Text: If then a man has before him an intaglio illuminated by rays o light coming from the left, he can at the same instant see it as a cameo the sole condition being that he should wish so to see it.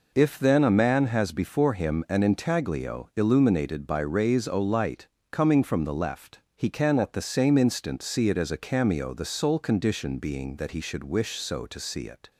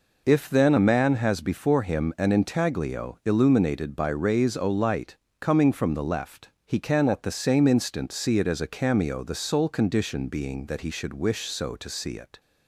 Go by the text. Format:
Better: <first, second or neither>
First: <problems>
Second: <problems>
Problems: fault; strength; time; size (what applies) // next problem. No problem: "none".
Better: neither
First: pauses between "light" and "coming"; slight; at 5.0 s; 0.24 s long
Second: pauses between "light" and "coming"; slight; at 5.1 s; 0.24 s long